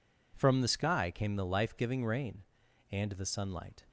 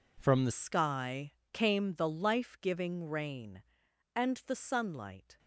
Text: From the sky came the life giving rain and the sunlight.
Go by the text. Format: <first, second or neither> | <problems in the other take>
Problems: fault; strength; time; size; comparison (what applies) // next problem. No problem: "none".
first | changes voice at "sky"; from 0.5 s on; 4.8 s long // pauses between "sky" and "came"; slight; at 1.3 s; 0.22 s long